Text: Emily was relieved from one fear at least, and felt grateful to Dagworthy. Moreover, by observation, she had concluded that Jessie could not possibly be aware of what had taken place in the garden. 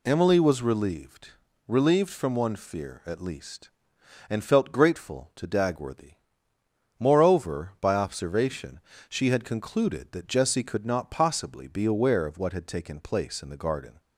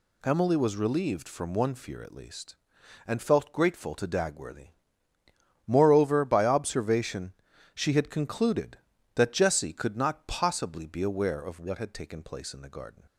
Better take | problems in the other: second | says "relieved" twice; at 1.6 s

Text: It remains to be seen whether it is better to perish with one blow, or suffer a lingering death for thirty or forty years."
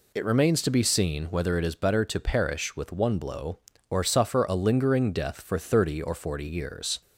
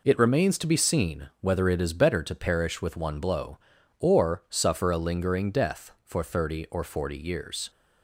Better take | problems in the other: neither | none

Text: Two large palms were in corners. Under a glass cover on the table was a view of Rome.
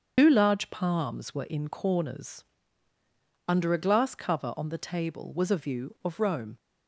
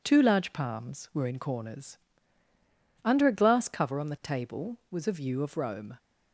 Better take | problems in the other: second | loses the start of "Two"; at 0.1 s; 105 ms // starts louder than the rest; until 1.1 s; 7 dB

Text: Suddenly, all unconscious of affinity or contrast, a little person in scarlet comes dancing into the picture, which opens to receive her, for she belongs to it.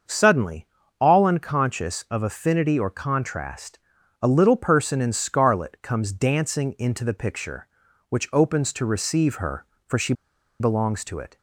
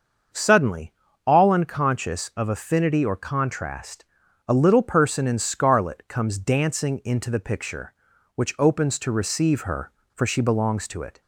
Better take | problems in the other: second | starts louder than the rest; until 1.4 s; 6.5 dB; also in the second // pauses between "she" and "belongs"; noticeable; at 10.1 s; 0.47 s long

